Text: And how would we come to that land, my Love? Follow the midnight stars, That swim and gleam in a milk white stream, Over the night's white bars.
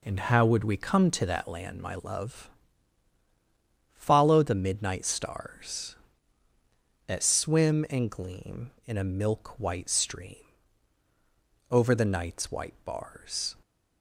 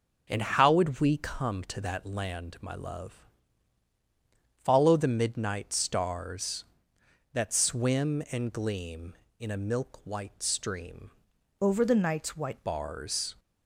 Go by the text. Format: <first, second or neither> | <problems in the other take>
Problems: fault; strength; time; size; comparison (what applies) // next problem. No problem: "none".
first | changes voice from "Over" to "white"; from 11.6 to 12.6 s; 1.0 s long